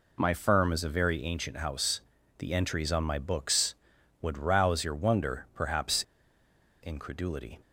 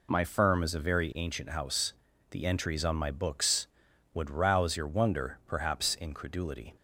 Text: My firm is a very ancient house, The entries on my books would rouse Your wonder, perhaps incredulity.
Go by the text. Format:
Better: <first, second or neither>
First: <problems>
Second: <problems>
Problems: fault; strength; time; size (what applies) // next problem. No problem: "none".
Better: second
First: pauses between "perhaps" and "incredulity"; noticeable; at 6.0 s; 0.83 s long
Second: none